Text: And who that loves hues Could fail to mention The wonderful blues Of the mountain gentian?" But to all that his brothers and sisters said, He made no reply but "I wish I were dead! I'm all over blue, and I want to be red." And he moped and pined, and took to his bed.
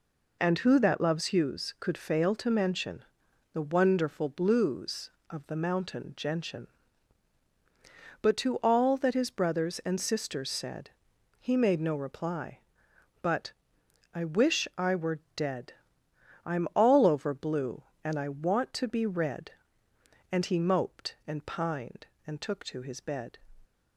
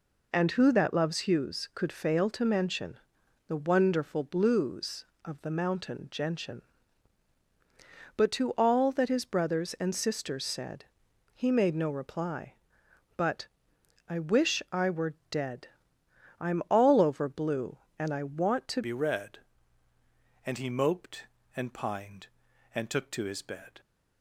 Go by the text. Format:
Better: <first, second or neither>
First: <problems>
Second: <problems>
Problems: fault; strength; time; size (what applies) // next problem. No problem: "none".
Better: first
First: pauses between "mention" and "The"; noticeable; at 3.0 s; 0.50 s long // pauses between "but" and "I"; noticeable; at 13.5 s; 0.62 s long // pauses between "were" and "dead"; slight; at 15.1 s; 0.16 s long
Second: pauses between "mention" and "The"; noticeable; at 2.9 s; 0.50 s long // pauses between "but" and "I"; noticeable; at 13.4 s; 0.62 s long // pauses between "were" and "dead"; slight; at 15.1 s; 0.16 s long // changes voice at "be"; from 18.8 s on; 4.9 s long